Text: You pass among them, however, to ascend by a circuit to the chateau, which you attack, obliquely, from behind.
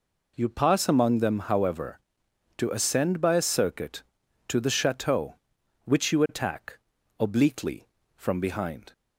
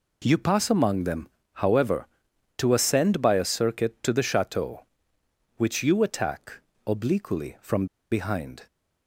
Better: first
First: none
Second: pauses between "from" and "behind"; slight; at 7.8 s; 0.26 s long

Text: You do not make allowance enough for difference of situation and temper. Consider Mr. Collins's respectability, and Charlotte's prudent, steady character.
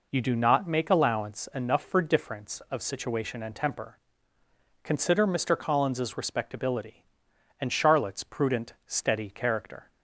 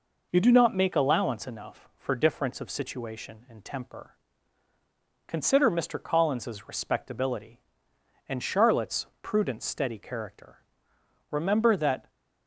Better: first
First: none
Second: pauses between "Charlotte's" and "prudent"; slight; at 9.0 s; 0.16 s long // goes on to say "Remember that"; noticeable; from 11.3 s on; 0.78 s long

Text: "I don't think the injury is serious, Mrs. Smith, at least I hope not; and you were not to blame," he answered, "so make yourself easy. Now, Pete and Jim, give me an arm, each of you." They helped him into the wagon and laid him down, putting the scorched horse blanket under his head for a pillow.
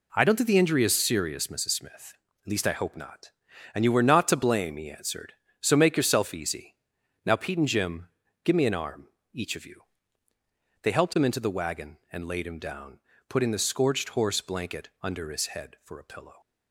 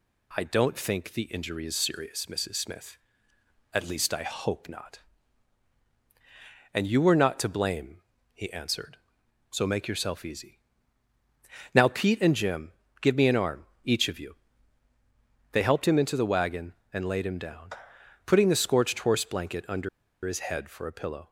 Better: first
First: none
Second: pauses between "under" and "his"; at 19.8 s; 0.36 s long

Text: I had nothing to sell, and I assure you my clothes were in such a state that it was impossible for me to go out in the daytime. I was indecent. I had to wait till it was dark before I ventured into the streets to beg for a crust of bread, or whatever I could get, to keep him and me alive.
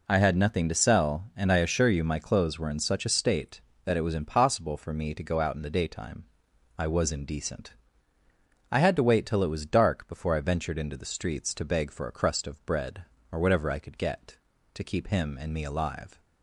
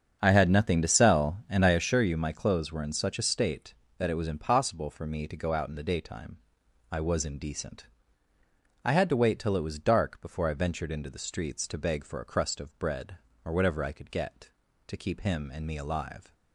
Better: first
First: none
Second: starts louder than the rest; strong; until 1.9 s; 7 dB

